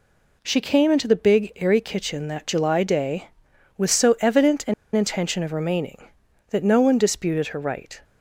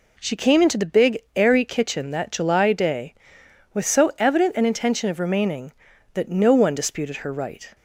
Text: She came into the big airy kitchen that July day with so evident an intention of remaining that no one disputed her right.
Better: second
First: pauses between "an" and "intention"; slight; at 4.7 s; 0.22 s long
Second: none

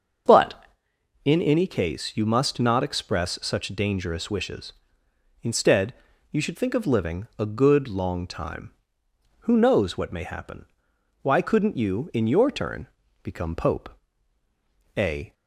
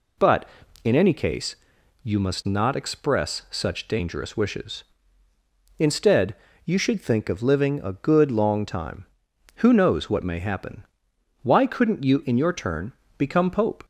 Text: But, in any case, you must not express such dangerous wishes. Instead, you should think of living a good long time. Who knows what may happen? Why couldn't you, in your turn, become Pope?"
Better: second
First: starts louder than the rest; until 1.8 s; 6.5 dB // goes on to say "A"; slight; from 14.9 s on; 0.36 s long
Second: none

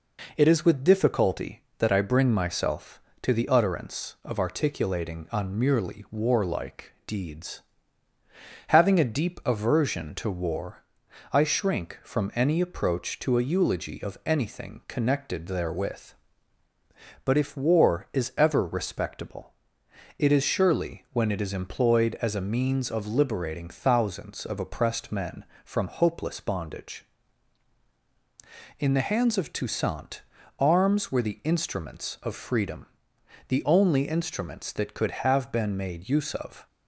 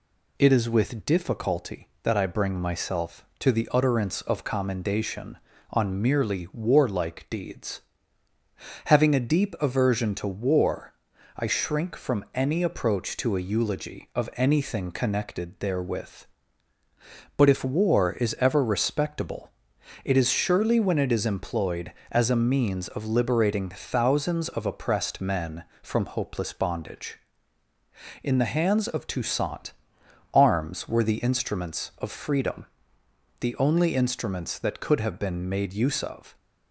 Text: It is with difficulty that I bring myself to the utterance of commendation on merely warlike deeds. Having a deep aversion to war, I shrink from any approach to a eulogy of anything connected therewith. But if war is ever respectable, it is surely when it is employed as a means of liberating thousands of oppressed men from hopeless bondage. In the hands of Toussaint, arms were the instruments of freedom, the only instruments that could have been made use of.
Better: second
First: says "articulating" for "commendation"; at 4.3 s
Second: none

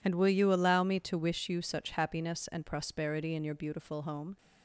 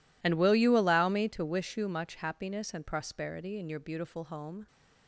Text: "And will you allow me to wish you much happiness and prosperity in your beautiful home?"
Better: second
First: says "such" for "much"; at 1.6 s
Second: none

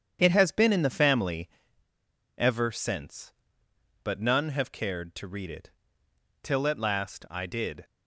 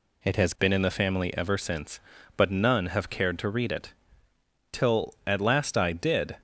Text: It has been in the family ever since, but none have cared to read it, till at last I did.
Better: second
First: starts louder than the rest; strong; until 1.2 s; 8 dB // pauses between "family" and "ever"; noticeable; at 1.4 s; 0.88 s long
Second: none

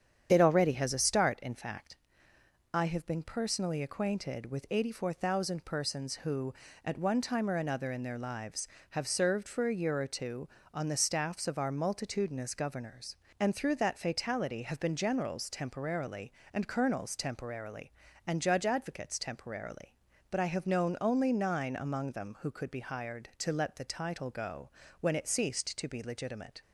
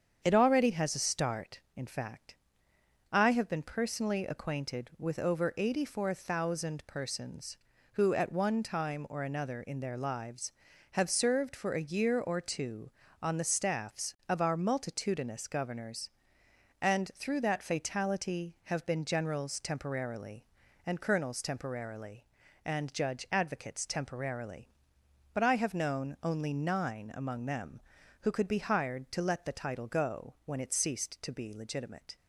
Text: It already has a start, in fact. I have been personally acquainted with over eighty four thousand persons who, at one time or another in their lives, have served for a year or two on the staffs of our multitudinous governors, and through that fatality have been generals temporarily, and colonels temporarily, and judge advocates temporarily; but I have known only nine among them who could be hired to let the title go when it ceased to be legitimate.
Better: second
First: starts louder than the rest; strong; until 1.3 s; 8.5 dB // skips "over"; at 4.6 s // pauses between "go" and "when"; slight; at 24.6 s; 0.32 s long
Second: starts louder than the rest; strong; until 1.2 s; 7.5 dB

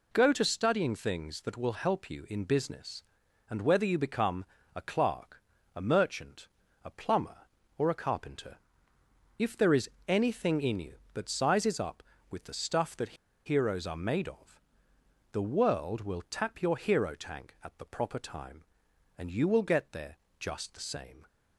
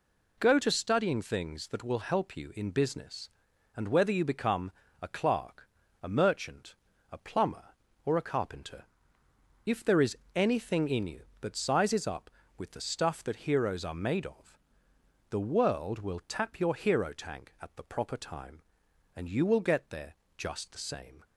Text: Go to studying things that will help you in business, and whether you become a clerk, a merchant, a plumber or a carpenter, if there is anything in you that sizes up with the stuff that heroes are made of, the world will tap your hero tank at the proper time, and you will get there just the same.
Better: second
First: pauses between "become" and "a"; slight; at 4.4 s; 0.32 s long // pauses between "is" and "anything"; slight; at 9.8 s; 0.20 s long // pauses between "that" and "heroes"; slight; at 13.1 s; 0.32 s long // pauses between "there" and "just"; slight; at 20.1 s; 0.22 s long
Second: pauses between "become" and "a"; slight; at 4.6 s; 0.32 s long // pauses between "is" and "anything"; slight; at 10.1 s; 0.20 s long // pauses between "there" and "just"; slight; at 20.1 s; 0.22 s long

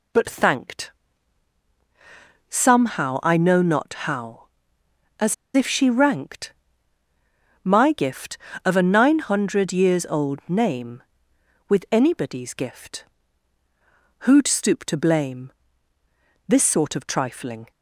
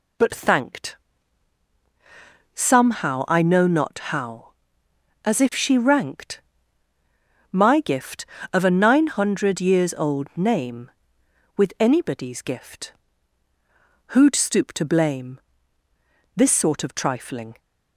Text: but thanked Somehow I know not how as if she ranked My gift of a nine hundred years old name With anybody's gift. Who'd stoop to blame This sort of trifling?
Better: second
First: pauses between "thanked" and "Somehow"; strong; at 0.9 s; 1.5 s long // pauses between "as" and "if"; slight; at 5.3 s; 0.19 s long // pauses between "ranked" and "My"; at 6.5 s; 1.1 s long // pauses between "blame" and "This"; noticeable; at 15.5 s; 0.96 s long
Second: pauses between "thanked" and "Somehow"; strong; at 0.9 s; 1.5 s long // pauses between "ranked" and "My"; at 6.4 s; 1.1 s long // pauses between "blame" and "This"; noticeable; at 15.3 s; 0.96 s long

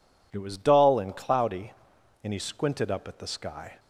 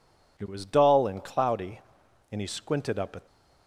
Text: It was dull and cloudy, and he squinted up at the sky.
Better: first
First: none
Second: stops before "the sky"; at 3.2 s

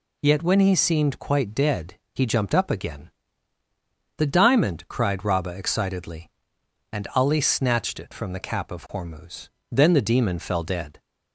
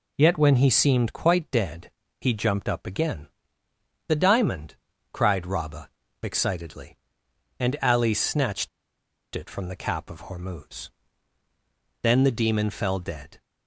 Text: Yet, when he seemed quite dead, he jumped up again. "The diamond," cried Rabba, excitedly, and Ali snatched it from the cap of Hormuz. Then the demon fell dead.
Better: first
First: none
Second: pauses between "snatched" and "it"; noticeable; at 8.6 s; 0.65 s long

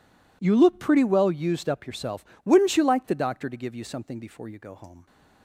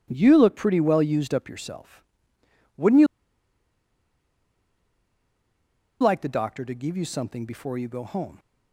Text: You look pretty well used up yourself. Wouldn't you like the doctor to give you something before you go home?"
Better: first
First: none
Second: pauses between "you" and "like"; strong; at 3.0 s; 2.9 s long

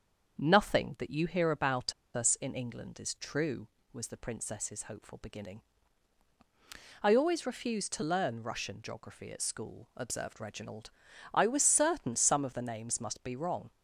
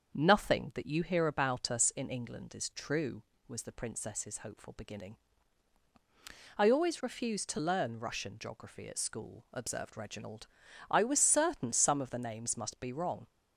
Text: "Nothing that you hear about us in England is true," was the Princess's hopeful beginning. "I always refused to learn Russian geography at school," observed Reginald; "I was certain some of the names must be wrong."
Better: second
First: starts louder than the rest; until 1.4 s; 7 dB // pauses between "about" and "us"; slight; at 1.9 s; 0.23 s long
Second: starts louder than the rest; until 1.1 s; 7 dB

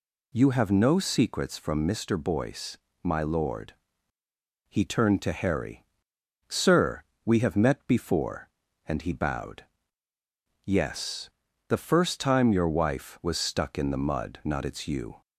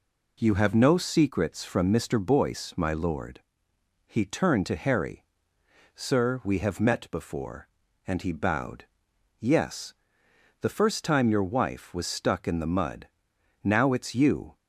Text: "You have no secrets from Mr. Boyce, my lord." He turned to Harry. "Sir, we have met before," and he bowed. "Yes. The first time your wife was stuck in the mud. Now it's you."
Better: second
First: says "Not" for "Now"; at 14.4 s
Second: none

